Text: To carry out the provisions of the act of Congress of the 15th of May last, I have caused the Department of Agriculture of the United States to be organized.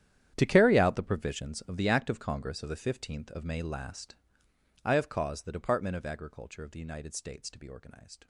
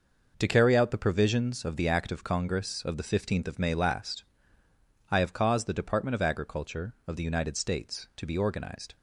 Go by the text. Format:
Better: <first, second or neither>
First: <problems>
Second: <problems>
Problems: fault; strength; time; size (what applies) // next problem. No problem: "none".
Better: second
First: gets quieter; strong; throughout; 16 dB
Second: none